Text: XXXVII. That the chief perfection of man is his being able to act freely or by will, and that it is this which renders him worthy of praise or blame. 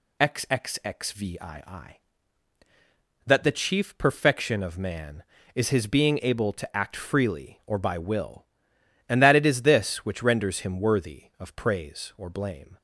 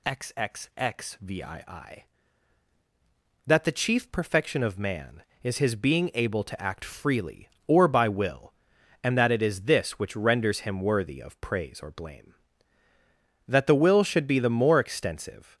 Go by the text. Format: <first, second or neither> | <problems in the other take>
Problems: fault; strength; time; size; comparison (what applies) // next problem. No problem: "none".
first | goes on to say "That the will should be the more extensive"; strong; from 13.4 s on; 2.1 s long